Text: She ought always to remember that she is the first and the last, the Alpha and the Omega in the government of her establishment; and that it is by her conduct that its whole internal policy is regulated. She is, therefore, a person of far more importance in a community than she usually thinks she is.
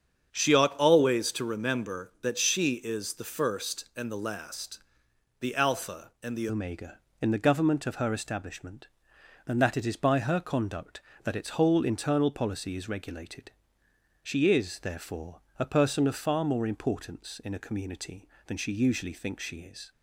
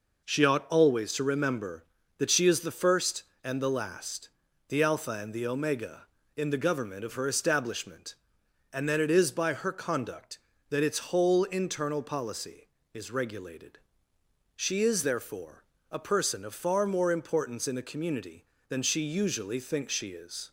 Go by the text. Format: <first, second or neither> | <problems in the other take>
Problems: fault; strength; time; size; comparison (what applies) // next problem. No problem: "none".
second | starts louder than the rest; strong; until 1.3 s; 8 dB // changes voice at "Omega"; from 6.4 s on; 13.5 s long